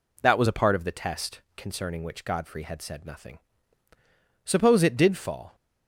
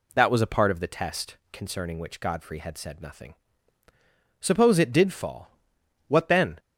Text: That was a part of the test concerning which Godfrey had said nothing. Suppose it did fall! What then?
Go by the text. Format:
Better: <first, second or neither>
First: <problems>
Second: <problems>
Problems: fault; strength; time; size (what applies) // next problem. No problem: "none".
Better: second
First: pauses between "test" and "concerning"; slight; at 1.4 s; 0.16 s long // stops before "What then"; at 5.5 s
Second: pauses between "test" and "concerning"; slight; at 1.3 s; 0.16 s long